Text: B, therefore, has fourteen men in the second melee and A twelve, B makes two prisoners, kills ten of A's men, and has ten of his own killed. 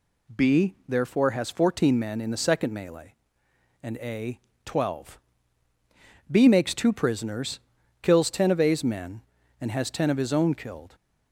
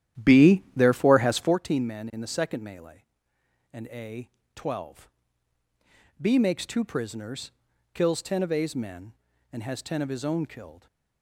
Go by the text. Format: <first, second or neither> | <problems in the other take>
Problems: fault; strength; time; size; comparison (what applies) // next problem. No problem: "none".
first | starts louder than the rest; strong; until 1.6 s; 11.5 dB // pauses between "A" and "twelve"; slight; at 4.2 s; 0.26 s long; slight in the first